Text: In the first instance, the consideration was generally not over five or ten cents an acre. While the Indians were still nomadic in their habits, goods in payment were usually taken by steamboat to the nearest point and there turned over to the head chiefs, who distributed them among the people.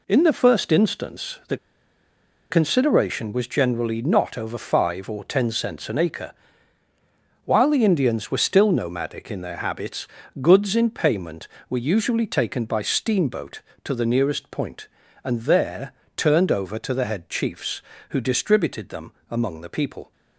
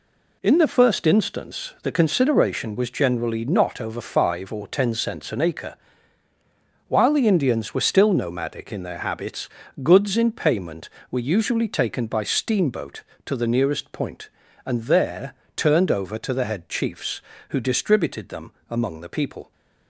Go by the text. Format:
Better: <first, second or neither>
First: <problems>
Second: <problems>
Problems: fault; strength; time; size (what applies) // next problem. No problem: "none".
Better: second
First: pauses between "the" and "consideration"; noticeable; at 1.5 s; 0.94 s long // pauses between "there" and "turned"; slight; at 15.9 s; 0.24 s long // pauses between "them" and "among"; slight; at 19.1 s; 0.18 s long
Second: pauses between "there" and "turned"; slight; at 15.3 s; 0.23 s long // pauses between "them" and "among"; slight; at 18.5 s; 0.18 s long